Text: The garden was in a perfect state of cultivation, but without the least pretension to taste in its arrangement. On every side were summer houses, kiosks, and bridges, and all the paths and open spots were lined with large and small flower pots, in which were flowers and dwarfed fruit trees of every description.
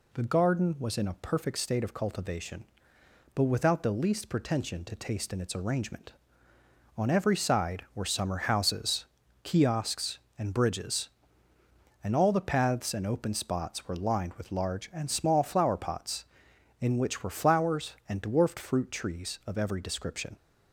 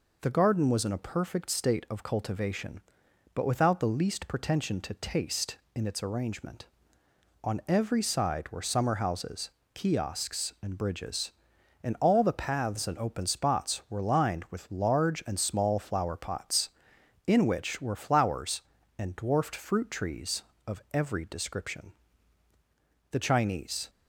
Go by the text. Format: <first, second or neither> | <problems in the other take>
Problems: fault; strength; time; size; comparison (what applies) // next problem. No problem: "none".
first | goes on to say "The Chinese"; noticeable; from 23.1 s on; 0.78 s long